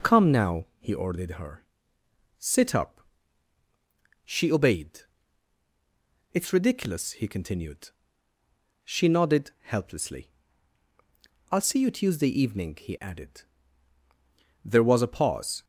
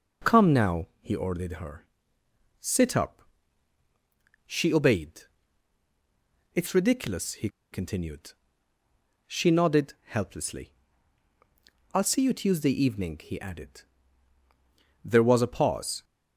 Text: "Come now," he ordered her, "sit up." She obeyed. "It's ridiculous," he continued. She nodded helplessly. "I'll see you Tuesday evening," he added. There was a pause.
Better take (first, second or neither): first